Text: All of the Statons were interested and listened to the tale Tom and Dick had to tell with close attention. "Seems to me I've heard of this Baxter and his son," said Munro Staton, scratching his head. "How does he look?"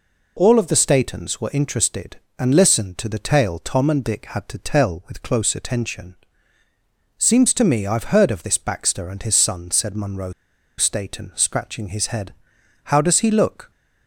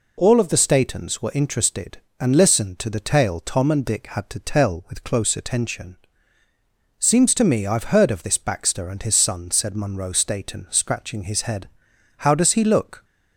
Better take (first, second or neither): second